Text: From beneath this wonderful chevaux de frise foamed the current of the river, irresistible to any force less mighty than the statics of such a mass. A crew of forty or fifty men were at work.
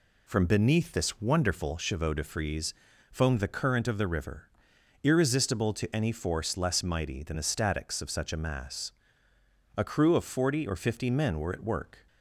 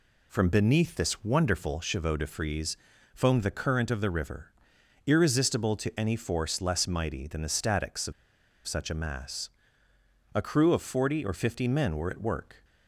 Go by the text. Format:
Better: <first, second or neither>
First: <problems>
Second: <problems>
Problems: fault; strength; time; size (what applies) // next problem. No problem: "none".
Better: first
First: pauses between "frise" and "foamed"; at 2.7 s; 0.38 s long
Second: pauses between "frise" and "foamed"; at 2.7 s; 0.38 s long // pauses between "of" and "such"; noticeable; at 8.1 s; 0.53 s long